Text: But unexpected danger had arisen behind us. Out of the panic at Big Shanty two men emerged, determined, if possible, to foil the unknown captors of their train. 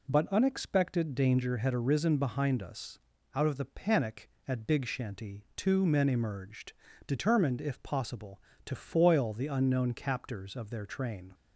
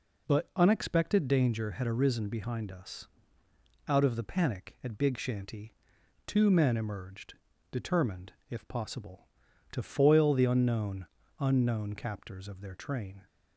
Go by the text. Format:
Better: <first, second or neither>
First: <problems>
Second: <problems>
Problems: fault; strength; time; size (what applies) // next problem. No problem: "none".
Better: first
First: none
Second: pauses between "Shanty" and "two"; noticeable; at 5.7 s; 0.50 s long // says "unknown" twice; at 11.3 s